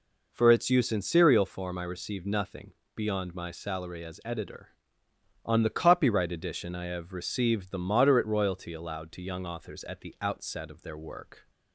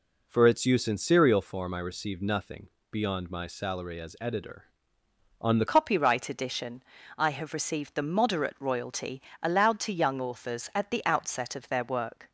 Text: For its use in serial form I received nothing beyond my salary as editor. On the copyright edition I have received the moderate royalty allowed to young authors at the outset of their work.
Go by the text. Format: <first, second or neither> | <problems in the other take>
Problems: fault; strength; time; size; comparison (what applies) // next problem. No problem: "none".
first | pauses between "nothing" and "beyond"; slight; at 2.6 s; 0.22 s long; slight in the first // changes voice at "copyright"; from 5.6 s on; 6.7 s long // pauses between "edition" and "I"; slight; at 6.8 s; 0.34 s long // pauses between "royalty" and "allowed"; slight; at 9.2 s; 0.20 s long